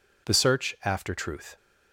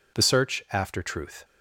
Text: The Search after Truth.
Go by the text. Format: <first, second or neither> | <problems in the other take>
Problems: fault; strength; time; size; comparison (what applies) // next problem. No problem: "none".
neither | none